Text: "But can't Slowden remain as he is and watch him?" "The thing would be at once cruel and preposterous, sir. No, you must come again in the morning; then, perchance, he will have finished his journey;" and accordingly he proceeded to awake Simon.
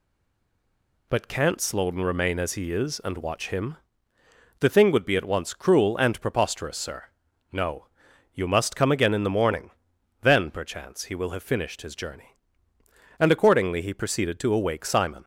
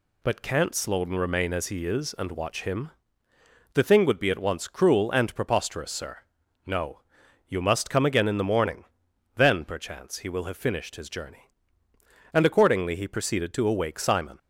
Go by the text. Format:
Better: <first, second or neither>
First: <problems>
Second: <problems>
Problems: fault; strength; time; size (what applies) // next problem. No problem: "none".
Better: second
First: stays silent before the first word; until 1.0 s; 1.0 s long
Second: none